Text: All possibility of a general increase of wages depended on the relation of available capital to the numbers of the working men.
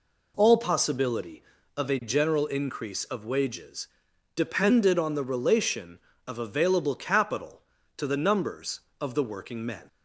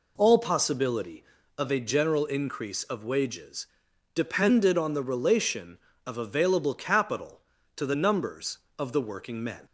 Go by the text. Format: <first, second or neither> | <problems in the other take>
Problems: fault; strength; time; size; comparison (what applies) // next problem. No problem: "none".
neither | pauses between "wages" and "depended"; noticeable; the same in both